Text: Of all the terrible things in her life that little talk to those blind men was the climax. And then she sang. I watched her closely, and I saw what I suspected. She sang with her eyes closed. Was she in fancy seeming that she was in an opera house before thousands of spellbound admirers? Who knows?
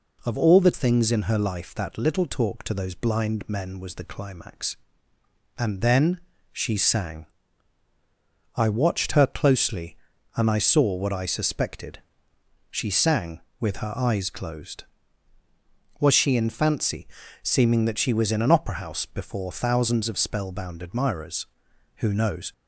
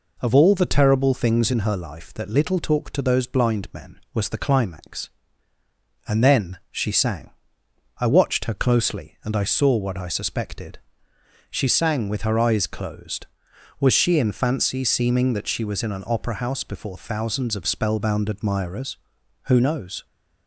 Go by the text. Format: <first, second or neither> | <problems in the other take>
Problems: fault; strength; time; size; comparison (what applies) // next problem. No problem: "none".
second | skips "terrible"; at 0.7 s // pauses between "then" and "she"; slight; at 6.2 s; 0.32 s long // pauses between "fancy" and "seeming"; slight; at 17.0 s; 0.36 s long